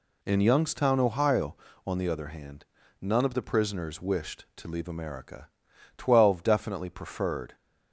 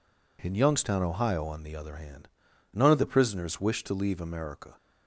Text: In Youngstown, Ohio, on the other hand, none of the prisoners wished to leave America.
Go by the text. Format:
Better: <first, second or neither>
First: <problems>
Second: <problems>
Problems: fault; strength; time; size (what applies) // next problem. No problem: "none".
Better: second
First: goes on to say "Twelve definitely preferred"; from 5.9 s on; 1.5 s long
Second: none